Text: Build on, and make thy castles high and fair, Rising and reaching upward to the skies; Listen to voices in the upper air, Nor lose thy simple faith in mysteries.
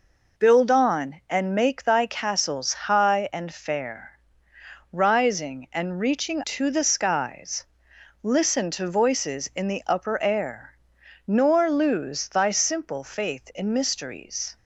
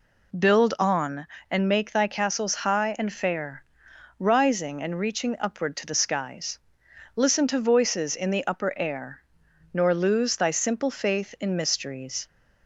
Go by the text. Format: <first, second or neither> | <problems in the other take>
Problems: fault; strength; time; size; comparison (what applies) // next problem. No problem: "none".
second | skips "upward"; at 6.4 s